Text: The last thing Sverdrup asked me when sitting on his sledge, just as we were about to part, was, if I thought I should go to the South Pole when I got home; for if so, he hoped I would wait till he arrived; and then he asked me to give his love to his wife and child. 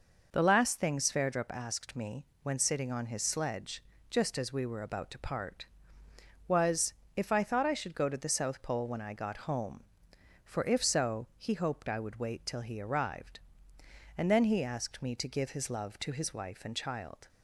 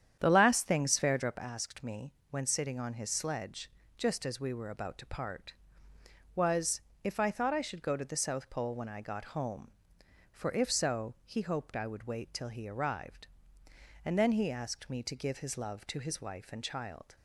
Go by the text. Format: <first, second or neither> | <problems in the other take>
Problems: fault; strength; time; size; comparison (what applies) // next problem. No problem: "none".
first | starts louder than the rest; strong; until 1.5 s; 9 dB // pauses between "me" and "when"; slight; at 2.1 s; 0.16 s long; slight in the first